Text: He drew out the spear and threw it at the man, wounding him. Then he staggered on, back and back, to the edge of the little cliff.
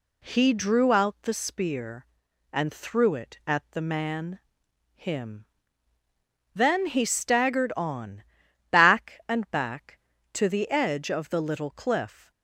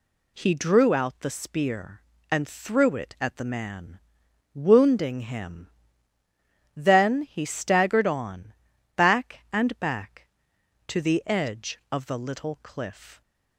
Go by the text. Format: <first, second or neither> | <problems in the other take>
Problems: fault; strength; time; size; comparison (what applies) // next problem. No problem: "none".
second | skips "wounding"; at 4.6 s